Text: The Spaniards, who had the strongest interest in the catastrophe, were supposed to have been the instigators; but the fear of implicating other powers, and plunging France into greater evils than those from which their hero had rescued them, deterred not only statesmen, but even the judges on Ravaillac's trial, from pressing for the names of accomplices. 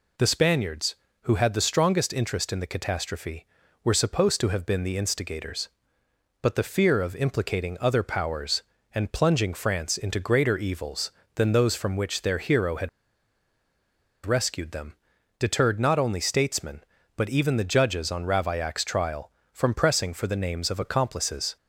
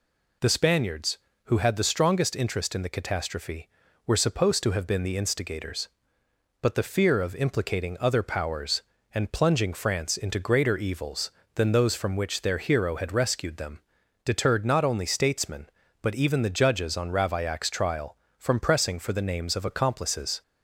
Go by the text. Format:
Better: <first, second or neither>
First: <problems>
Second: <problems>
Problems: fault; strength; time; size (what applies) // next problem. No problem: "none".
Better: second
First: pauses between "had" and "rescued"; strong; at 12.8 s; 1.3 s long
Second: none